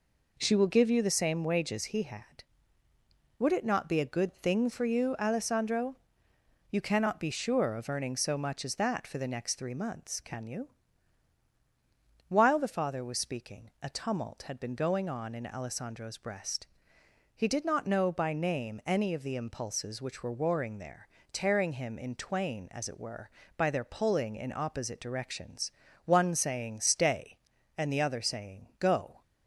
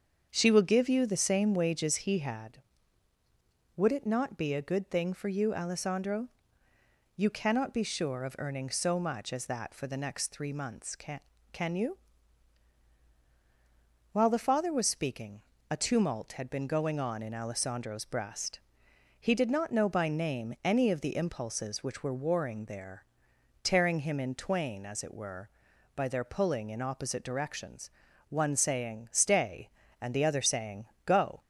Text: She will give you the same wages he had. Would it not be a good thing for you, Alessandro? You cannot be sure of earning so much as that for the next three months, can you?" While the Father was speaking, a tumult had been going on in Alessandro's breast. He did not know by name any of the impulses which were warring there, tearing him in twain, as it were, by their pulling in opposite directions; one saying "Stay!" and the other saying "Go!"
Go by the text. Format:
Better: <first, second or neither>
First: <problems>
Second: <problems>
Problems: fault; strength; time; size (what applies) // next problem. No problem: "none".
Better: first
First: none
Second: starts louder than the rest; until 1.3 s; 7 dB // says "can" twice; at 11.5 s // pauses between "saying" and "Go"; slight; at 30.8 s; 0.22 s long